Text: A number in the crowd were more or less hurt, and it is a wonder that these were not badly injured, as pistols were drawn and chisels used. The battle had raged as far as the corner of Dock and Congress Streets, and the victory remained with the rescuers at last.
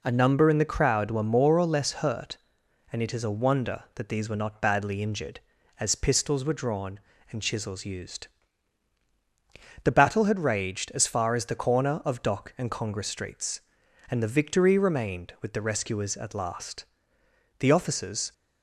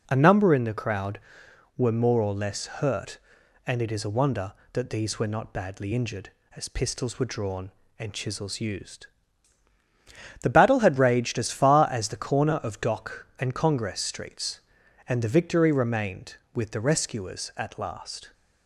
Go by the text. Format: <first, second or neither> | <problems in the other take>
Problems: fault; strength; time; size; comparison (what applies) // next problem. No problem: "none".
second | goes on to say "The officers"; noticeable; from 17.5 s on; 0.74 s long